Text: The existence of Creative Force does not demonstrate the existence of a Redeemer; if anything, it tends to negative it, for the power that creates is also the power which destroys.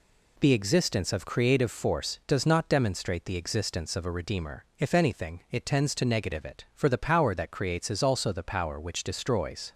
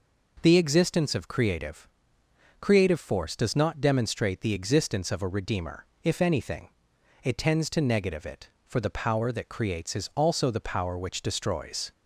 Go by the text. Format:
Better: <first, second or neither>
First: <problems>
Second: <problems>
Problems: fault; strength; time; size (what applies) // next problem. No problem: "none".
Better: first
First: none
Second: says "Creative" twice; at 2.5 s